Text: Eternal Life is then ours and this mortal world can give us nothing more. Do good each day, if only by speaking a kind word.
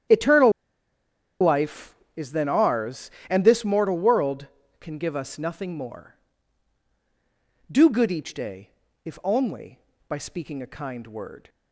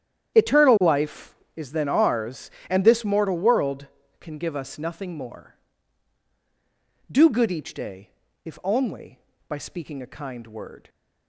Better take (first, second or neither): second